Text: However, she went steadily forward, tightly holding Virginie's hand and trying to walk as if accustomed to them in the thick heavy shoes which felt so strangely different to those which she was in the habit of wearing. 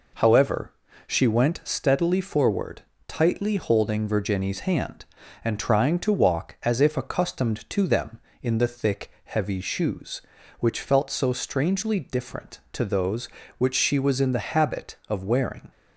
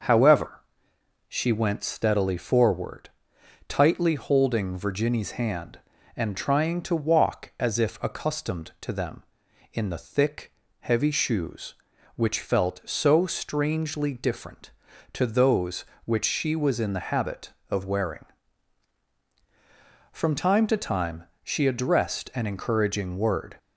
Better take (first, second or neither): first